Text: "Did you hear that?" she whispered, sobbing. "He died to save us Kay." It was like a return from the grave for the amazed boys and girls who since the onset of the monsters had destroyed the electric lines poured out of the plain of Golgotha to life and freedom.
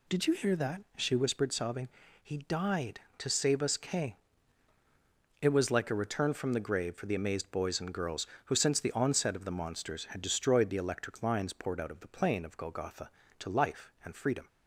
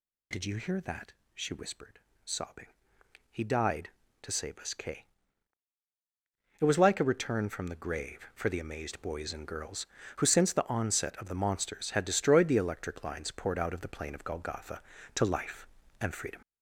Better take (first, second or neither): first